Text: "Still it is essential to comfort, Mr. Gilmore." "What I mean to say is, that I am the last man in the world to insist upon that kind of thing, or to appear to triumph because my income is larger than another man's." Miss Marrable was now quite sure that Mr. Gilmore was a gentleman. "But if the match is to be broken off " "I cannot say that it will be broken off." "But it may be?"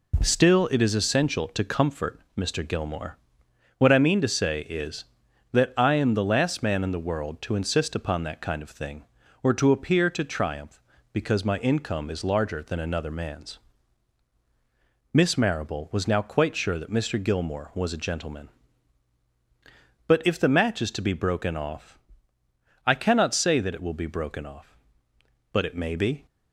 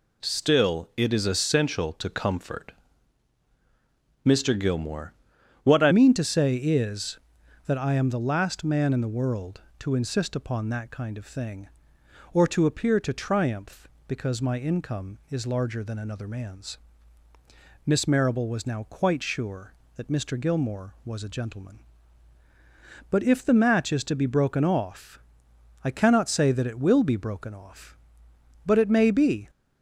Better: first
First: none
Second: changes voice at "mean"; from 5.9 s on; 23.5 s long

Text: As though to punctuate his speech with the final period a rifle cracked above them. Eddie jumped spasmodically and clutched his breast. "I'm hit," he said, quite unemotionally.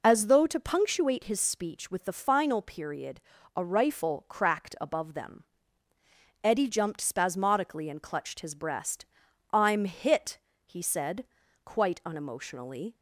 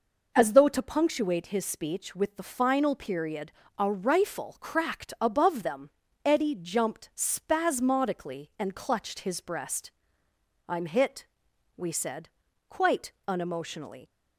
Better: first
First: pauses between "period" and "a"; slight; at 3.2 s; 0.34 s long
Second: pauses between "period" and "a"; slight; at 3.5 s; 0.26 s long // says "we" for "he"; at 11.7 s // pauses between "quite" and "unemotionally"; slight; at 13.1 s; 0.16 s long

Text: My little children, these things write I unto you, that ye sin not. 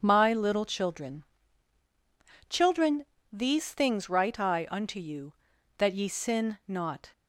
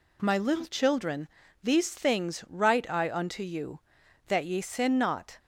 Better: second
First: starts louder than the rest; strong; until 1.0 s; 7.5 dB // says "children" twice; at 2.4 s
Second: none

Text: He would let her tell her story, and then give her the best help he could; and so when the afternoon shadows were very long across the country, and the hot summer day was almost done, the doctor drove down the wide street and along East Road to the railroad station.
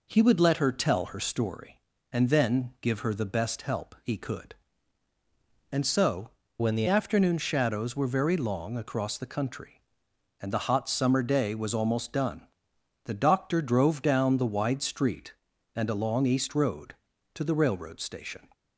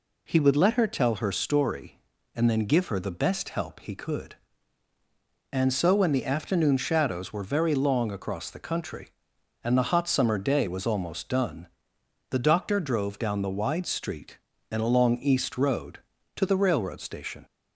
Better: second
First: changes voice from "when" to "the"; from 6.5 to 6.8 s; 0.3 s long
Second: none

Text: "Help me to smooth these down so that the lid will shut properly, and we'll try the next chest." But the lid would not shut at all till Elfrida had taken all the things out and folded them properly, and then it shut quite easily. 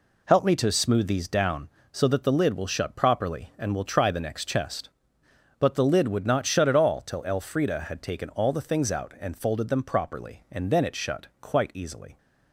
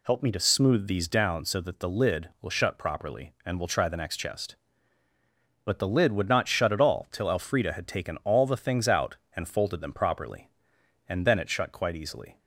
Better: neither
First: none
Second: none

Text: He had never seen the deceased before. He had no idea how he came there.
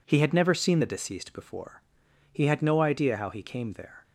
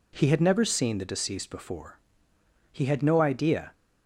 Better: first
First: none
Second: stops before "how he came there"; at 3.7 s

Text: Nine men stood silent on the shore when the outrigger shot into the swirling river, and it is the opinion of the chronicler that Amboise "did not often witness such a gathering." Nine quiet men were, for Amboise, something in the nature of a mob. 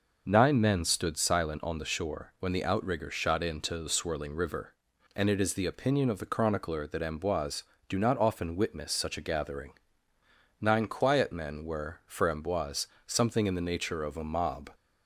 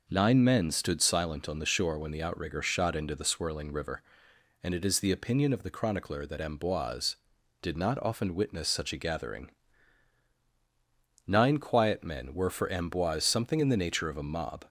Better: second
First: says "do" for "did"; at 7.8 s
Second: none

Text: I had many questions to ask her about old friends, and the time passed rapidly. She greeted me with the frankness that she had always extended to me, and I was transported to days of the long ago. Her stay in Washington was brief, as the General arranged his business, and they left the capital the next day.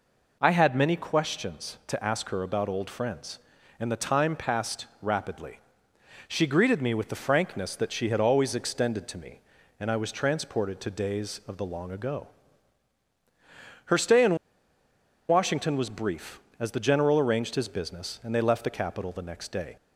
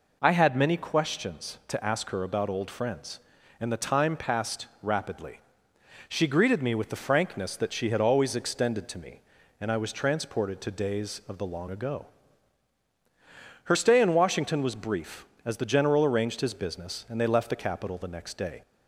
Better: second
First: pauses between "passed" and "rapidly"; slight; at 4.8 s; 0.16 s long // pauses between "in" and "Washington"; noticeable; at 14.3 s; 0.92 s long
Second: pauses between "passed" and "rapidly"; slight; at 4.6 s; 0.16 s long

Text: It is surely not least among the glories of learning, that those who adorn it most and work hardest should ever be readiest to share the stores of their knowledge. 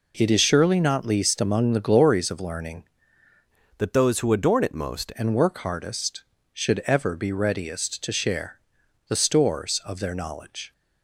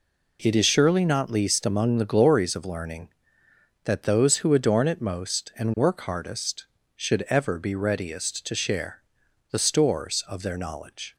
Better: second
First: changes voice from "that" to "most"; from 3.7 to 5.1 s; 1.4 s long // pauses between "share" and "the"; noticeable; at 8.6 s; 0.48 s long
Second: pauses between "share" and "the"; noticeable; at 9.0 s; 0.48 s long

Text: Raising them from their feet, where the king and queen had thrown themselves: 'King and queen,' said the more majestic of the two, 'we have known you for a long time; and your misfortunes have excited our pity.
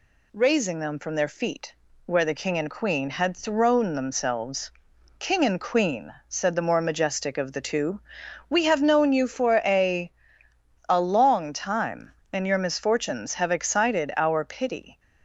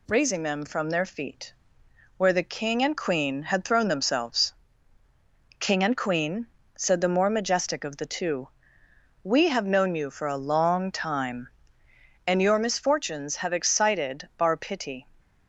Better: second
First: says "a" twice; at 10.8 s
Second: none

